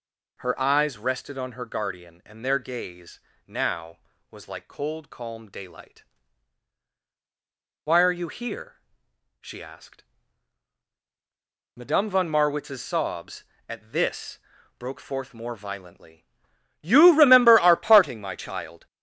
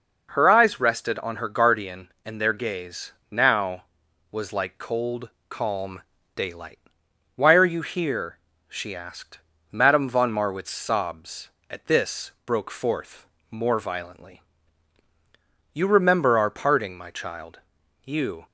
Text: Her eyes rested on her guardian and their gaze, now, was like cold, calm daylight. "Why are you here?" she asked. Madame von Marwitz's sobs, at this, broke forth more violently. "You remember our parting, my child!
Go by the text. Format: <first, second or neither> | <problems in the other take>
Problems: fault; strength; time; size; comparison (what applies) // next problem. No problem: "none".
first | pauses between "calm" and "daylight"; slight; at 6.0 s; 0.32 s long // pauses between "forth" and "more"; slight; at 13.2 s; 0.24 s long // goes on to say "You"; slight; from 18.0 s on; 0.42 s long